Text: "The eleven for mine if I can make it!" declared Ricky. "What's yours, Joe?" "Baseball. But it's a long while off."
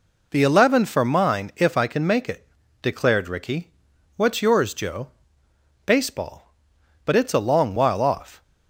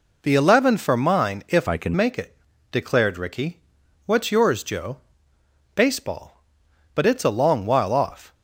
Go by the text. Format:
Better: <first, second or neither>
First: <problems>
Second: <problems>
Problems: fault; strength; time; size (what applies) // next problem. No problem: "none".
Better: first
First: none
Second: changes voice from "I" to "can"; from 1.6 to 1.9 s; 0.3 s long